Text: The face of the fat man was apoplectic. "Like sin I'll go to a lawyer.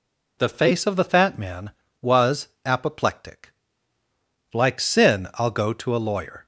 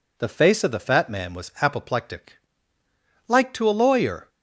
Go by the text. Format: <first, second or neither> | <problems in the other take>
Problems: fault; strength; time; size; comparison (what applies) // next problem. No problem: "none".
first | skips "sin I'll go"; at 3.5 s